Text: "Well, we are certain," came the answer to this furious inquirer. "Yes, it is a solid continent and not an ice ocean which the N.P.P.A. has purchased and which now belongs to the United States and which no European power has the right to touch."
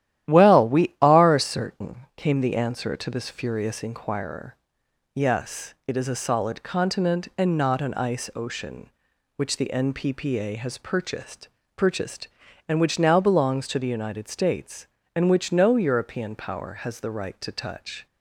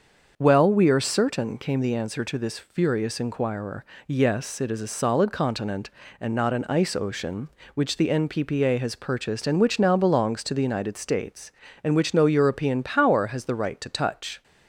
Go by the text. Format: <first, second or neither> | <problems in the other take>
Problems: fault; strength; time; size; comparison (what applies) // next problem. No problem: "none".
second | starts louder than the rest; strong; until 1.3 s; 12.5 dB; also in the second // says "purchased" twice; at 11.7 s